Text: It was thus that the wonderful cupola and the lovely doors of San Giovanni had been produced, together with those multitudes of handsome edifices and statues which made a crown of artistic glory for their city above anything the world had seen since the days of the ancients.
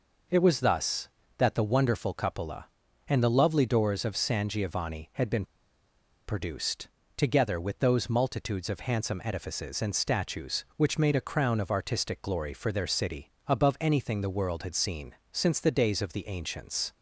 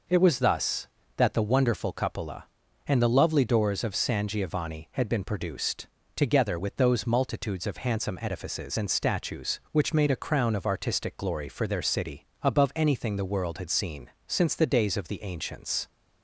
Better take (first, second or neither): second